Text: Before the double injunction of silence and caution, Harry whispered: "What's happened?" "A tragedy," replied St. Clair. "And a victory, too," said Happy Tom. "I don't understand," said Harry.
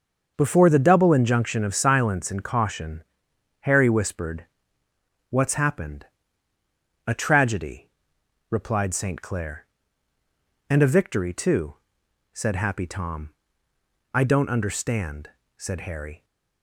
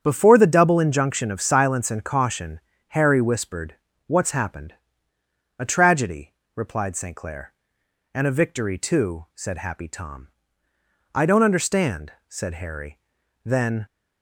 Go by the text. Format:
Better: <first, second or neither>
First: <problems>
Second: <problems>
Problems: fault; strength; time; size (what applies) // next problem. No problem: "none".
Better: first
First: starts louder than the rest; until 1.3 s; 6.5 dB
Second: starts louder than the rest; strong; until 1.0 s; 8 dB // goes on to say "Then"; slight; from 13.4 s on; 0.40 s long